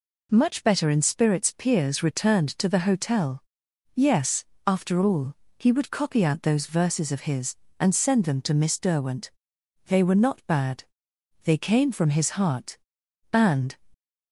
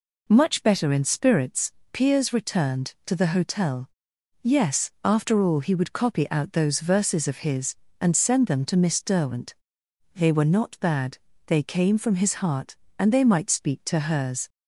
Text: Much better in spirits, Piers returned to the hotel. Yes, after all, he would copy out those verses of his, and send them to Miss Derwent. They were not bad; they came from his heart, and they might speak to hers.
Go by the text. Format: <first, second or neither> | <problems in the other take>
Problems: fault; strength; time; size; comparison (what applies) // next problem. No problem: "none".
second | stops before "they might speak to hers"; at 13.9 s